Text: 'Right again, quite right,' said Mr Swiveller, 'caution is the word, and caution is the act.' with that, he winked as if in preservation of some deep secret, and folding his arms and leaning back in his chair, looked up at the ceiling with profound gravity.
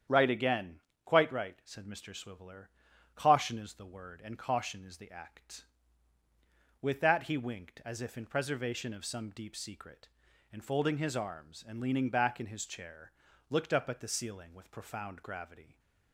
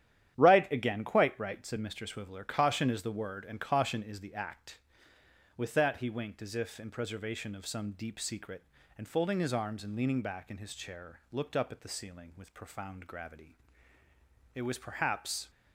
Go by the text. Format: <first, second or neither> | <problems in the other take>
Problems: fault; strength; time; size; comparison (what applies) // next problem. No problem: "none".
first | starts louder than the rest; strong; until 1.4 s; 10.5 dB; strong in the first // goes on to say "It was perhaps"; noticeable; from 14.5 s on; 0.94 s long